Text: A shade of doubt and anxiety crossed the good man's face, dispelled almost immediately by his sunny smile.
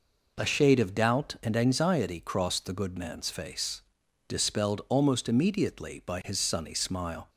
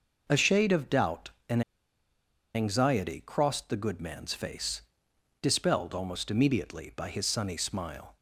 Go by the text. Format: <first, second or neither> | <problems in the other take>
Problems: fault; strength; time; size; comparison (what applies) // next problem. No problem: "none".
first | pauses between "and" and "anxiety"; noticeable; at 1.6 s; 0.93 s long